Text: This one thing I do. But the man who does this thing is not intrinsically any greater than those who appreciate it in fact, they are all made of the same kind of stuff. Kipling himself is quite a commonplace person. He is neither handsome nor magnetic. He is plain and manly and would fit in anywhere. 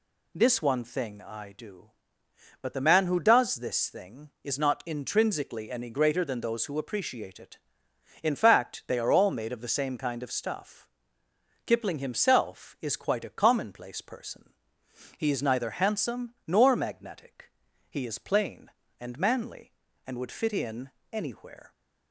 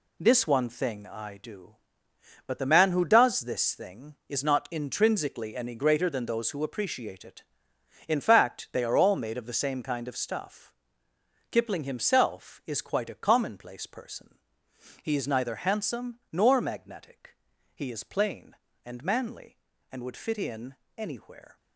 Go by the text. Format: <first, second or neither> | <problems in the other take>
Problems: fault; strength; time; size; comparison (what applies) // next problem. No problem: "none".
first | gets quieter; strong; throughout; 8.5 dB // pauses between "in" and "anywhere"; slight; at 20.7 s; 0.24 s long; slight in the first